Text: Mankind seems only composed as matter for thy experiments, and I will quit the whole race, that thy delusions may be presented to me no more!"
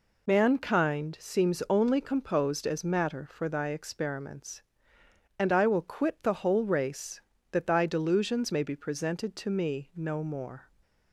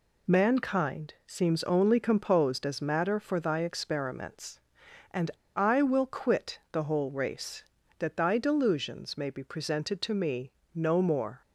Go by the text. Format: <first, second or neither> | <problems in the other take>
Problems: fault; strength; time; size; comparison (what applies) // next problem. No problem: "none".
first | pauses between "and" and "I"; slight; at 5.2 s; 0.26 s long // pauses between "me" and "no"; slight; at 10.5 s; 0.24 s long